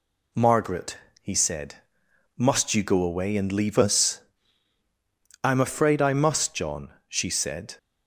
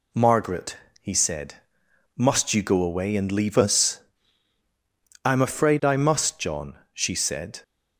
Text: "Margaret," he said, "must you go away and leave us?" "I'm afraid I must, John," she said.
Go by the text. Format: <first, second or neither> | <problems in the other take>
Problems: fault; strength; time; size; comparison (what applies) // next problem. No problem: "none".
neither | none